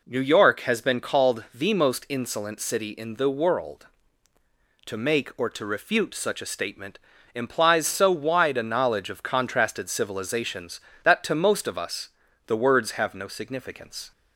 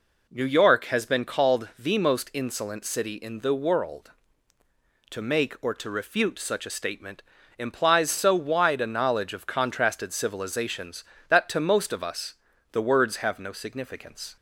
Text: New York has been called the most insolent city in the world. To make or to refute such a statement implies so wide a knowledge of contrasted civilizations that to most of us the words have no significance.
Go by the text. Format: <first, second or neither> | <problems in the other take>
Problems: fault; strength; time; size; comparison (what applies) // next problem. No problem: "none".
neither | pauses between "statement" and "implies"; slight; the same in both // pauses between "us" and "the"; the same in both